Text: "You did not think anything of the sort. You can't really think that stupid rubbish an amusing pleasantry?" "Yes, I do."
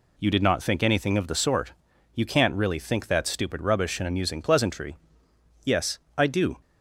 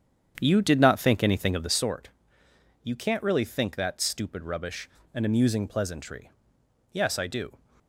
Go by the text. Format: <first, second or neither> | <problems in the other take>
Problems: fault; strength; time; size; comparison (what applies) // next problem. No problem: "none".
first | starts louder than the rest; strong; until 1.8 s; 8.5 dB // pauses between "rubbish" and "an"; slight; at 4.8 s; 0.28 s long